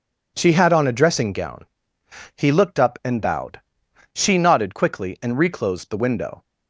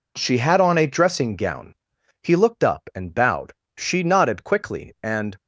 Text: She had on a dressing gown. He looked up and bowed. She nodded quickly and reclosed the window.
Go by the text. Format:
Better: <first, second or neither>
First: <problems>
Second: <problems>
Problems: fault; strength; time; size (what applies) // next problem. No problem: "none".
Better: first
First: none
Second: stops before "reclosed the window"; at 5.3 s